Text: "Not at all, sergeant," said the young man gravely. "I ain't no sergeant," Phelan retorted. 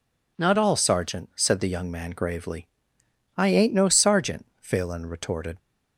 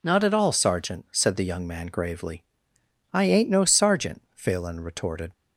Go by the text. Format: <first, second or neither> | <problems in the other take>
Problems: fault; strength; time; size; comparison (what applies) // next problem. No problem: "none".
second | skips "at"; at 0.5 s